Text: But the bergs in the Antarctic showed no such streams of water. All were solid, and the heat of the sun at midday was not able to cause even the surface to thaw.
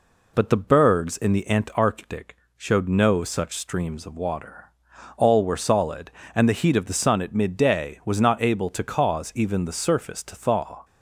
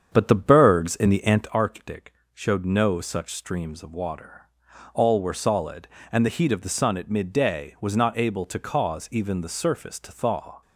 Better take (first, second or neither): first